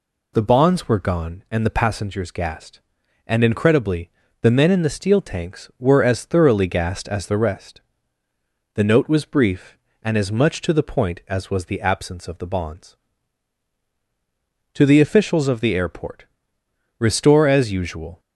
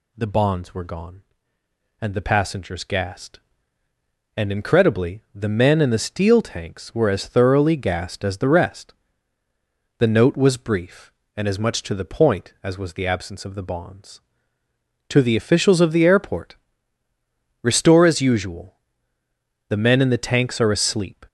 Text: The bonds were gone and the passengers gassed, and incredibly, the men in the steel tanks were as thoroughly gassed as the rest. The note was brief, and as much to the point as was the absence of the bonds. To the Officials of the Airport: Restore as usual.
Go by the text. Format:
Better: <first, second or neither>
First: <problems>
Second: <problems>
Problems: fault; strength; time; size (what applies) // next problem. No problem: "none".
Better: first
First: none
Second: goes on to say "The men in the tanks are asleep"; from 19.6 s on; 1.5 s long